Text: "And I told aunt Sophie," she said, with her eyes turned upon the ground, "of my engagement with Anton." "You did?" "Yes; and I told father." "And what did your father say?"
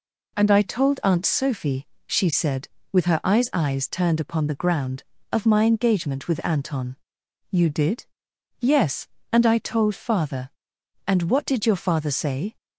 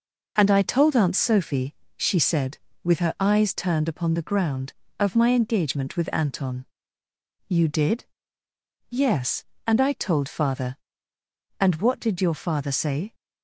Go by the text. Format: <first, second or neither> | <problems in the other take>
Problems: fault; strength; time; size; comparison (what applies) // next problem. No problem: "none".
second | says "eyes" twice; at 3.5 s